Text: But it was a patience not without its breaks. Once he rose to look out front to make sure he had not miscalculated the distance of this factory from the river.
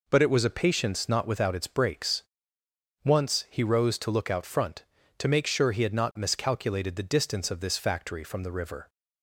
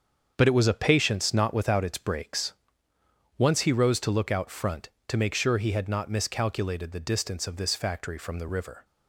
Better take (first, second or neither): first